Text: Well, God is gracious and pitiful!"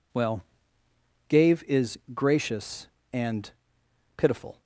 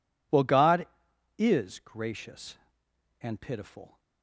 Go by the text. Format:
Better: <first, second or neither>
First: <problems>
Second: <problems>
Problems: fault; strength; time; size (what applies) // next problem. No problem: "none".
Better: second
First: says "Gave" for "God"; at 1.2 s // pauses between "and" and "pitiful"; noticeable; at 3.4 s; 0.66 s long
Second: none